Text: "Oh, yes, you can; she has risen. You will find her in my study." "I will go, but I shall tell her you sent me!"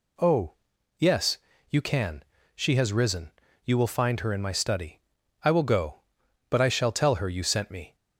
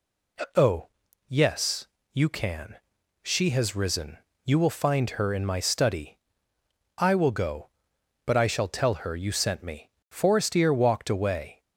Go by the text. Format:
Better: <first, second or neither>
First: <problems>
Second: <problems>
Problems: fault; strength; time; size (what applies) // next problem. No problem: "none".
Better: first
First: none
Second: goes on to say "Forestier walked away"; from 10.0 s on; 1.5 s long